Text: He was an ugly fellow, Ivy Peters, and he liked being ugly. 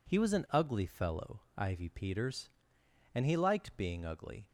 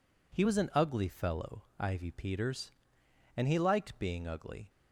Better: neither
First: none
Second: none

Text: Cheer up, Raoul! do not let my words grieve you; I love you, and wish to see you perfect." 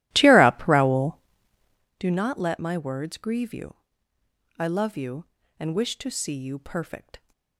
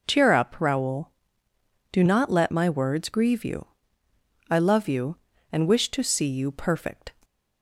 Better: second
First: starts louder than the rest; strong; until 2.0 s; 15 dB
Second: none

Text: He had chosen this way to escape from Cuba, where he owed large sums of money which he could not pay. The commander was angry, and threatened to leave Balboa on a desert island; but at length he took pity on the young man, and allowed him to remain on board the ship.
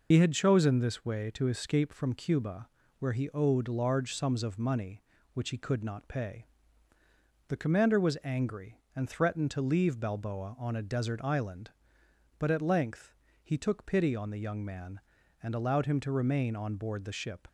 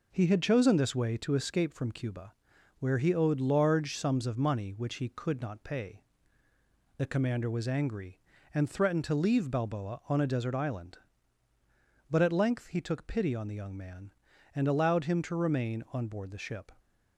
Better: second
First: loses the start of "He"; at 0.1 s; 55 ms // pauses between "length" and "he"; slight; at 13.1 s; 0.30 s long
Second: none

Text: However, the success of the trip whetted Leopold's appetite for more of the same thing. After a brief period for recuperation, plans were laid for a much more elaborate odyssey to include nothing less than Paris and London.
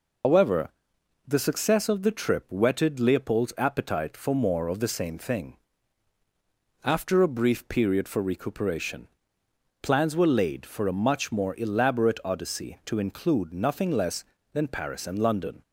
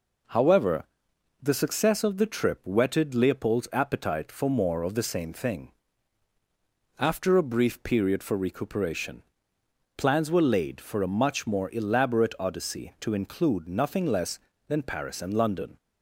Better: second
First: loses the start of "However"; at 0.2 s; 130 ms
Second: none

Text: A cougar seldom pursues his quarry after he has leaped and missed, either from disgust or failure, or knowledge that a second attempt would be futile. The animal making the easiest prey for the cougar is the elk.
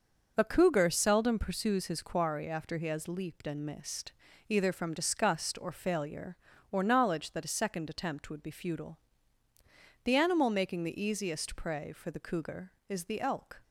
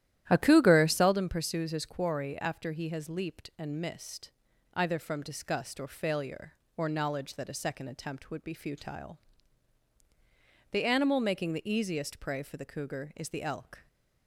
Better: first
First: none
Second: starts louder than the rest; strong; until 1.2 s; 12.5 dB

